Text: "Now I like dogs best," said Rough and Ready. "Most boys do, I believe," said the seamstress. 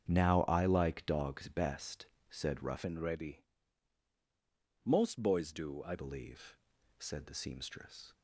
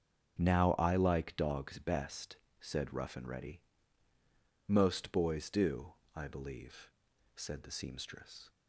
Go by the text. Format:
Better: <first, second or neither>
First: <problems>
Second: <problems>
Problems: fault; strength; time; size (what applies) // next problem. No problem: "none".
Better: second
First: starts louder than the rest; strong; until 1.0 s; 7.5 dB // changes voice from "and" to "I"; from 2.8 to 5.9 s; 3.1 s long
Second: starts louder than the rest; until 1.4 s; 6.5 dB